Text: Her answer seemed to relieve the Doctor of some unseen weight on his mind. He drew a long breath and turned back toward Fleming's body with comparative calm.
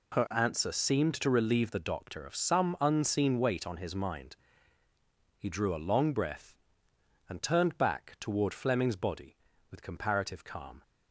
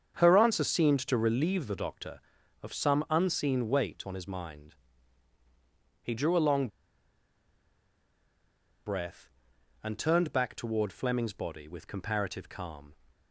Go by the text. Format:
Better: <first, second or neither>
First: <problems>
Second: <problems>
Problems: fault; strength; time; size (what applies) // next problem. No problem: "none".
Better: first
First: none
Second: starts louder than the rest; strong; until 1.2 s; 7.5 dB // pauses between "long" and "breath"; strong; at 6.6 s; 2.1 s long